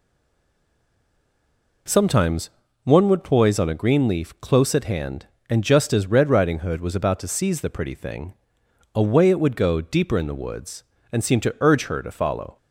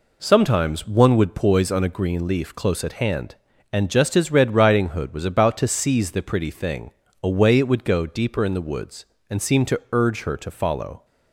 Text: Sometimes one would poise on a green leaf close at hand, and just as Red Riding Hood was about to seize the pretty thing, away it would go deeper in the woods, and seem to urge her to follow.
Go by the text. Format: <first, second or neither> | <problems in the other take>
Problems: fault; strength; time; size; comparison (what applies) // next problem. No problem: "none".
second | stays silent before the first word; noticeable; until 1.8 s; 1.8 s long // pauses between "Sometimes" and "one"; slight; at 2.4 s; 0.34 s long